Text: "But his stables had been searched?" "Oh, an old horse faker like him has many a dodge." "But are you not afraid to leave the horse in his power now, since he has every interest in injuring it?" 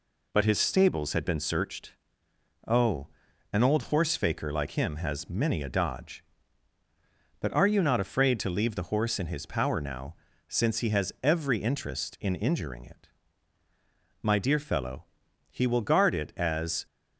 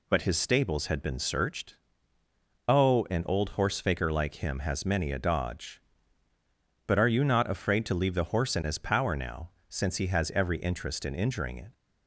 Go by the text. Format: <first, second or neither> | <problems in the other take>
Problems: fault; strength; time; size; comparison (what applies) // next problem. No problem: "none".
second | goes on to say "My dear fellow he will guard it as"; strong; from 14.2 s on; 2.6 s long